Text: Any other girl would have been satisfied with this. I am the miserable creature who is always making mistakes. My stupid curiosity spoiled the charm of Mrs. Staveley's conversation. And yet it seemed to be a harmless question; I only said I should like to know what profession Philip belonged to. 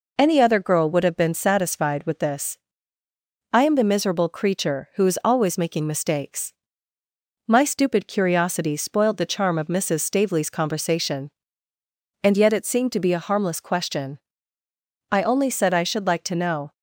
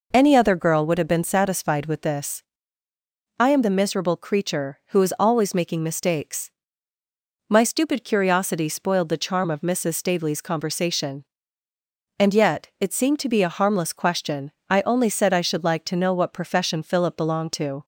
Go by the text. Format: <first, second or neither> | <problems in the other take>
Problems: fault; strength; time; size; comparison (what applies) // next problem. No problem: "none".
second | stops before "what profession Philip belonged to"; at 16.7 s